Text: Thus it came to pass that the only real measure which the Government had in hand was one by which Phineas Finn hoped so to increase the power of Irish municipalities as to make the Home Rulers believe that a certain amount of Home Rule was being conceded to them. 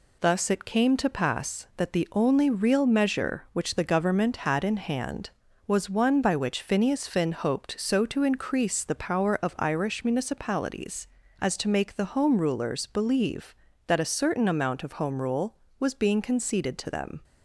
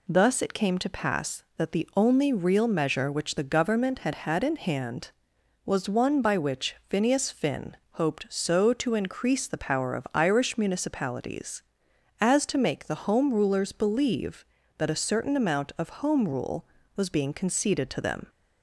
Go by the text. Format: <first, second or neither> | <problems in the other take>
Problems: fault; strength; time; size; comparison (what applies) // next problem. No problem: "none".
first | says "had" twice; at 4.1 s // pauses between "which" and "Phineas"; slight; at 6.7 s; 0.16 s long // pauses between "Finn" and "hoped"; slight; at 7.7 s; 0.16 s long